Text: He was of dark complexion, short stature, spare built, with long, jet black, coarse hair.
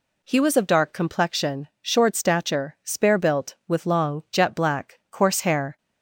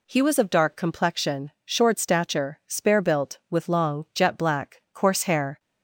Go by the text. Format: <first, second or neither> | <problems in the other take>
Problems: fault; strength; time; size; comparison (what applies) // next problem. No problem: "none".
neither | none